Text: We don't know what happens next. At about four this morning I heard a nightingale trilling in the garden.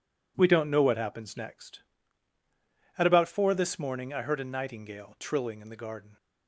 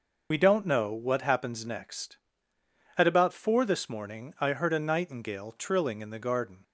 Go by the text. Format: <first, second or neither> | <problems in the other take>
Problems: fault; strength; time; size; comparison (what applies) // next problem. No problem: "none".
first | loses the start of "We"; at 0.3 s; 55 ms